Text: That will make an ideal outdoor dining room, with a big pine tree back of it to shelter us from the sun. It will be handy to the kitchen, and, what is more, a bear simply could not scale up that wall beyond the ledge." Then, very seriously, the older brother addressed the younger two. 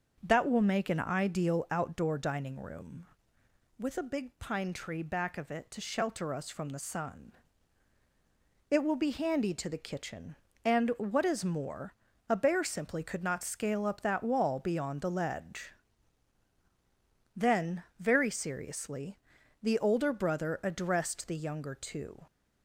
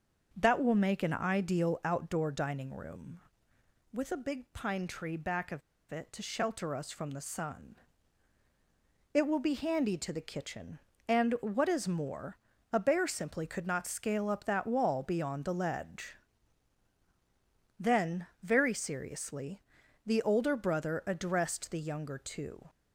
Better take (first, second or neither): first